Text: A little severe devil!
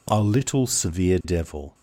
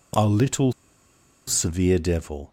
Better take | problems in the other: first | pauses between "little" and "severe"; noticeable; at 0.7 s; 0.77 s long

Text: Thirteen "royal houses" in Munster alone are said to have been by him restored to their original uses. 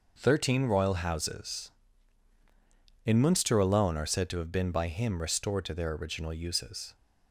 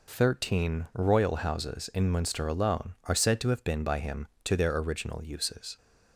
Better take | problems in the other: first | skips "restored"; at 4.3 s

